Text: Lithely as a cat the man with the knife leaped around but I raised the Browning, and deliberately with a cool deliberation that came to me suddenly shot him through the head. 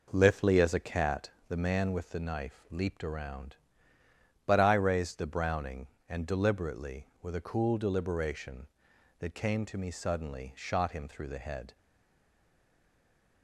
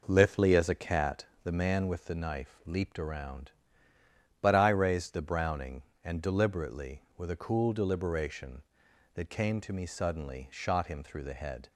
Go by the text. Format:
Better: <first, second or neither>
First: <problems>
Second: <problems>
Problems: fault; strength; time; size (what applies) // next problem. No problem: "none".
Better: second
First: pauses between "cat" and "the"; slight; at 1.2 s; 0.20 s long // stays silent after the last word; noticeable; from 11.7 s on; 1.7 s long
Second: pauses between "cat" and "the"; slight; at 1.2 s; 0.20 s long